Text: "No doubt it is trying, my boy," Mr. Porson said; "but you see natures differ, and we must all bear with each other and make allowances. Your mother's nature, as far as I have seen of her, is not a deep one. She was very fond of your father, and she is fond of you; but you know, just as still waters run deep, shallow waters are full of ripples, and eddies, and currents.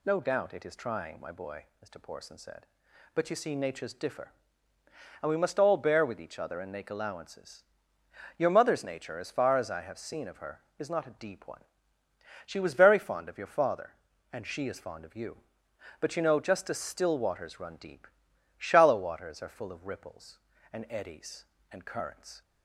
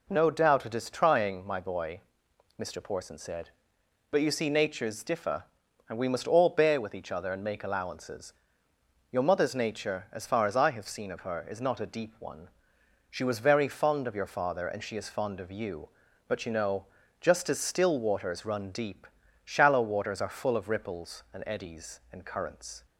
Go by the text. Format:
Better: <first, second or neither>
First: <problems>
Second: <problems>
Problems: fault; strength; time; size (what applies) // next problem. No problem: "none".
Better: neither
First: none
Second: none